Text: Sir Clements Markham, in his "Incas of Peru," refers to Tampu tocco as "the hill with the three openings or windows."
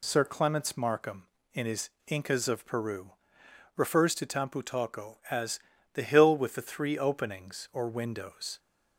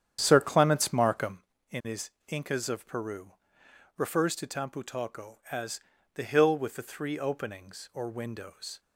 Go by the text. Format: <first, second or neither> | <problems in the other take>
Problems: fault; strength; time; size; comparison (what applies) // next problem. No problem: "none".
first | starts louder than the rest; strong; until 1.4 s; 9 dB // pauses between "his" and "Incas"; slight; at 2.0 s; 0.20 s long; slight in the first // pauses between "as" and "the"; slight; at 5.8 s; 0.32 s long; slight in the first